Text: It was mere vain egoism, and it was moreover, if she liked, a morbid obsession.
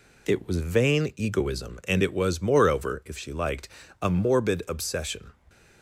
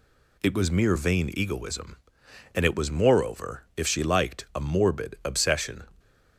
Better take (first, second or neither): second